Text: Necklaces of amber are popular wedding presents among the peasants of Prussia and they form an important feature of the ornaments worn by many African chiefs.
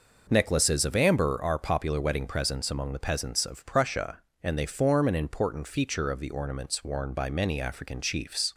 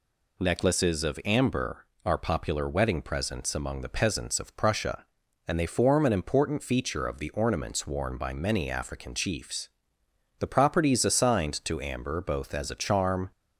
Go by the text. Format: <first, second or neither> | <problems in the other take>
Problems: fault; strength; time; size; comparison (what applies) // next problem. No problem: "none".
first | goes on to say "The properties assigned to amber both as a charm"; strong; from 10.3 s on; 2.9 s long